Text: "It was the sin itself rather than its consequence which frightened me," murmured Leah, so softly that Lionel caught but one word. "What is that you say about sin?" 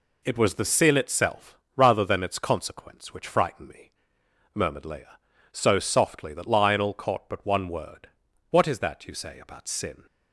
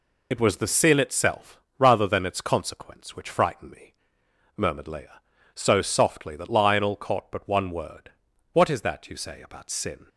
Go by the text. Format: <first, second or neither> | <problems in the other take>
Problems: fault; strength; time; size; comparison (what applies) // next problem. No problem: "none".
first | loses the start of "It"; at 0.3 s; 45 ms // pauses between "itself" and "rather"; slight; at 1.6 s; 0.18 s long; slight in the first